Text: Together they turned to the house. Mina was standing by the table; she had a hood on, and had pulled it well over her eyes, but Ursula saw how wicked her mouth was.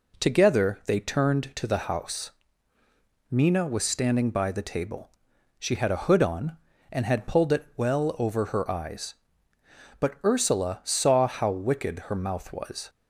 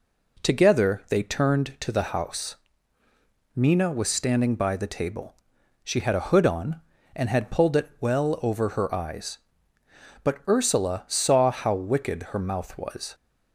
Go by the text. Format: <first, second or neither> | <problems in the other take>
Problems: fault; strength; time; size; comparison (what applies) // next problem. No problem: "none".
neither | none